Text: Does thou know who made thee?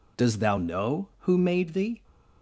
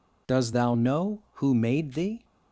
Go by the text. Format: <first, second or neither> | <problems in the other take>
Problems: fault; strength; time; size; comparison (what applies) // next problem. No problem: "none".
neither | none